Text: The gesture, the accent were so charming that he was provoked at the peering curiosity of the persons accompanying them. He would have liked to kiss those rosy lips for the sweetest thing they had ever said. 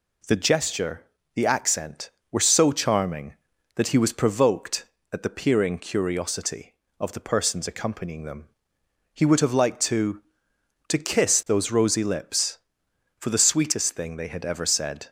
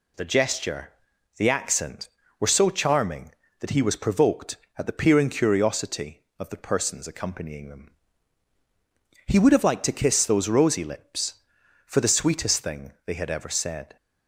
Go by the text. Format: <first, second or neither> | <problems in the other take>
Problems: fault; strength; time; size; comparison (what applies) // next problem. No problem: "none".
second | says "to" twice; at 10.8 s